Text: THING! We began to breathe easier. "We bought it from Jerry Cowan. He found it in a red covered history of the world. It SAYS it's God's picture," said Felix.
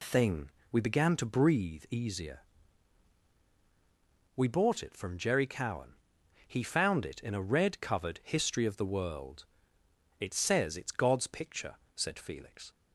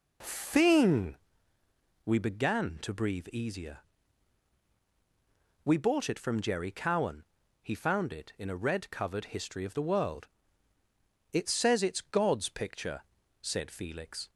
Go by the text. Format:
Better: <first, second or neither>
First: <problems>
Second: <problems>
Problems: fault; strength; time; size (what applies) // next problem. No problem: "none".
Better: neither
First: none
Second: none